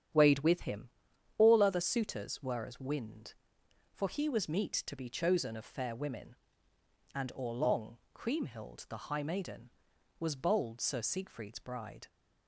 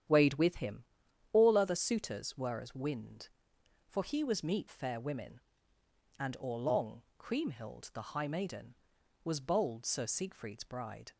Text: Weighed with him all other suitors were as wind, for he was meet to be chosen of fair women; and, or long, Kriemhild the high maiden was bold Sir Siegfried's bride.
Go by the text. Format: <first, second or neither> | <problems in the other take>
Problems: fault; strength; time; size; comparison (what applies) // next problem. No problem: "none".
first | starts louder than the rest; strong; until 1.5 s; 9.5 dB; strong in the first // pauses between "him" and "all"; noticeable; at 0.8 s; 0.50 s long; noticeable in the first // skips "to be chosen of"; at 4.6 s